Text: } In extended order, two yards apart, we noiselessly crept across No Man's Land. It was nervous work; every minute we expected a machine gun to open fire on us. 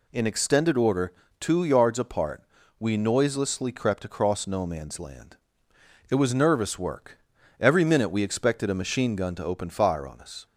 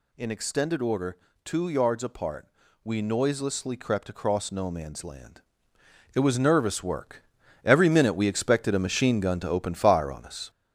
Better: first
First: none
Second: gets louder; noticeable; throughout; 5.5 dB

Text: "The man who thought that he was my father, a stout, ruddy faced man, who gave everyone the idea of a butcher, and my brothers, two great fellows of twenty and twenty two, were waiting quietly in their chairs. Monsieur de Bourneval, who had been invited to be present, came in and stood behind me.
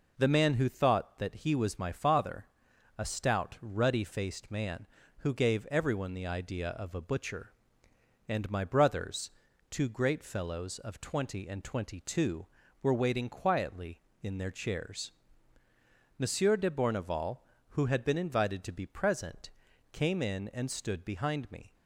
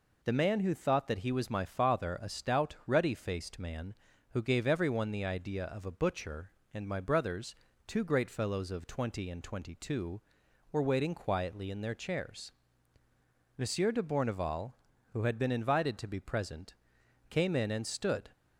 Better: first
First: none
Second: stops before "behind me"; at 18.3 s

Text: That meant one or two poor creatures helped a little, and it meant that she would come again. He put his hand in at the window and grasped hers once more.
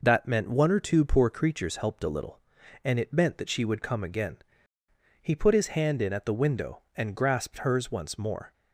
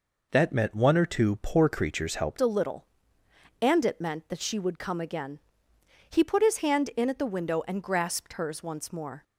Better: first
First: none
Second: changes voice at "a"; from 2.4 s on; 6.8 s long

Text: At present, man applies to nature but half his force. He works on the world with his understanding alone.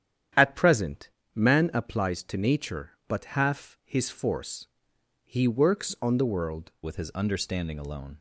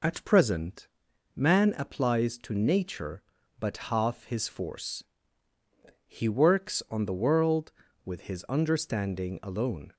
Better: second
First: starts louder than the rest; strong; until 1.5 s; 10 dB // changes voice at "with"; from 6.8 s on; 1.3 s long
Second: none

